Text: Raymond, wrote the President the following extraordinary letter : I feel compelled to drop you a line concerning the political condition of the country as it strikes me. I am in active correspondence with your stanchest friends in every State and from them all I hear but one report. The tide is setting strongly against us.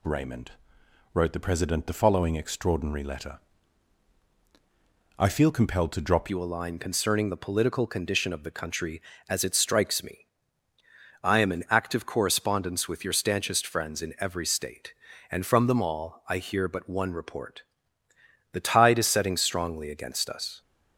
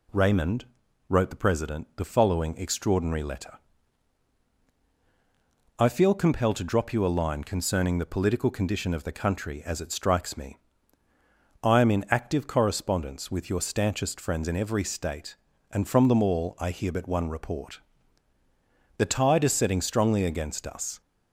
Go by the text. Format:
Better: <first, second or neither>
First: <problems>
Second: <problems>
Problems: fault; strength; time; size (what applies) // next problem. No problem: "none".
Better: second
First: changes voice at "you"; from 6.2 s on; 14.4 s long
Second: none